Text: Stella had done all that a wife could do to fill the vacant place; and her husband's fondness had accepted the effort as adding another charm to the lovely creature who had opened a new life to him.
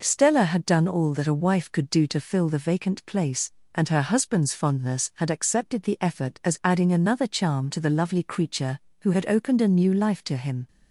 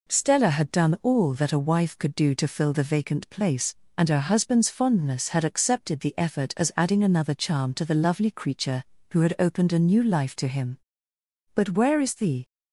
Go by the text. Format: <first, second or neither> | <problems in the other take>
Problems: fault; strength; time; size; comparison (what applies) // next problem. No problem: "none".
first | goes on to say "But where is the"; noticeable; from 11.5 s on; 0.90 s long